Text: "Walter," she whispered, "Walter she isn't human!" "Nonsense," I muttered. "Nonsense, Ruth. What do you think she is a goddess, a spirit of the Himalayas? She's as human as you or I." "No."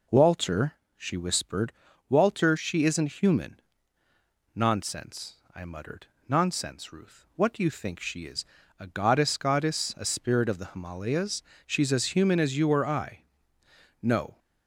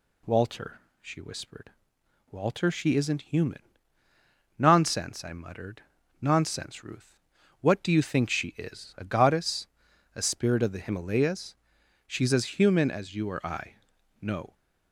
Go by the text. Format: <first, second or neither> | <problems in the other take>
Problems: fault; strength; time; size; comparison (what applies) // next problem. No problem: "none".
second | pauses between "is" and "a"; slight; at 8.4 s; 0.32 s long // says "goddess" twice; at 9.3 s